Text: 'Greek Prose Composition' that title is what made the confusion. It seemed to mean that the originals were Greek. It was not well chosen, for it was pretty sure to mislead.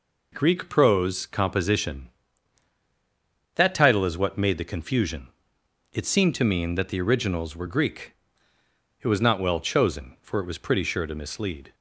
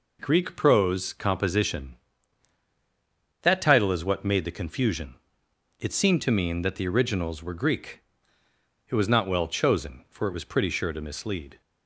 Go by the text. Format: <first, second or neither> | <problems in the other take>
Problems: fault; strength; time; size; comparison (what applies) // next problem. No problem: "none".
neither | none